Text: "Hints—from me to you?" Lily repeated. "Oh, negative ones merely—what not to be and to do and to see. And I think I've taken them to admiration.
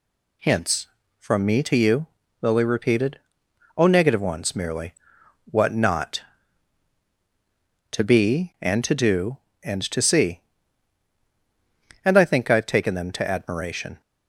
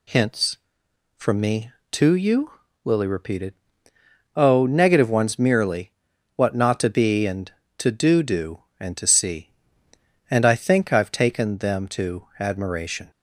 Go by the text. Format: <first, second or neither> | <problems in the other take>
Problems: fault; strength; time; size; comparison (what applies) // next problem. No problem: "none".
first | says "do" twice; at 8.2 s